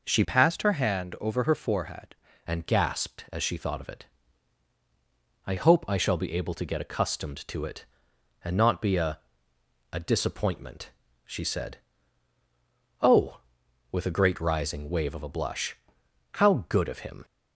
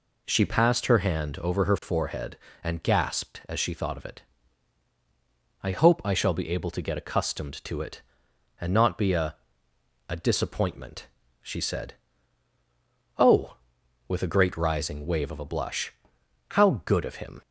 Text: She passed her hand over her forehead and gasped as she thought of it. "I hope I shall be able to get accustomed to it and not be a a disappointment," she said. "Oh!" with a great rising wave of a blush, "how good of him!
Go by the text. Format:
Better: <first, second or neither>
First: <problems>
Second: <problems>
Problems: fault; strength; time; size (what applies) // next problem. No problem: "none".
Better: second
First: changes voice from "passed" to "forehead"; from 0.2 to 2.1 s; 1.9 s long // pauses between "a" and "a"; noticeable; at 9.1 s; 0.72 s long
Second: pauses between "a" and "a"; noticeable; at 9.3 s; 0.72 s long